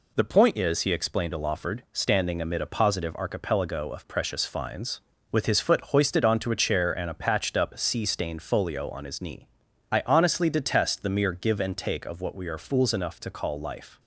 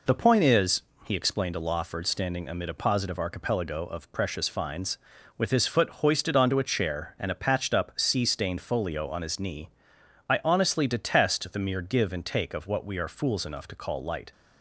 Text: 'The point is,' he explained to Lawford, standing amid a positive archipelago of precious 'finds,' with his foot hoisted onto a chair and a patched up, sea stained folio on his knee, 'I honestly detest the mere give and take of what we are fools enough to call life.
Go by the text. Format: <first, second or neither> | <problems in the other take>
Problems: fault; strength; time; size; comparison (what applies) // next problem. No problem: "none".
first | says "light" for "life"; at 14.0 s